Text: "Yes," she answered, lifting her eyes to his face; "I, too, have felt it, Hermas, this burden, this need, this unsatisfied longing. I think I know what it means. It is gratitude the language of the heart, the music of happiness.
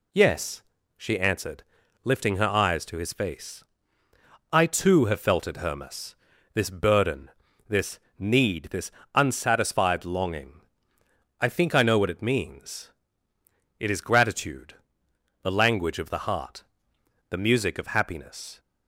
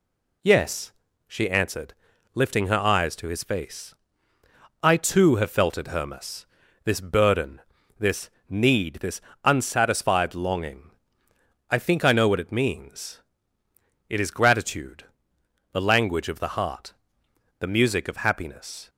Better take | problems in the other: neither | pauses between "this" and "need"; slight; the same in both // pauses between "this" and "unsatisfied"; slight; the same in both // pauses between "gratitude" and "the"; noticeable; the same in both

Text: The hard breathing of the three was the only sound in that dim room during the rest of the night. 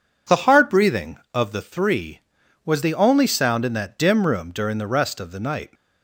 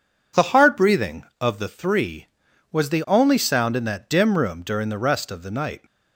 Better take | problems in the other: neither | none

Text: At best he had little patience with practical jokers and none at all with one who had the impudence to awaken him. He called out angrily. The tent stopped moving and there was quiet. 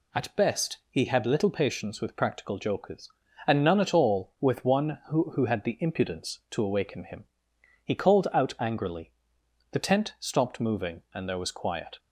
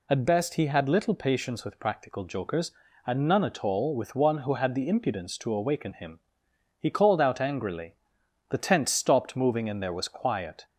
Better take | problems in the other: second | says "who" twice; at 5.3 s

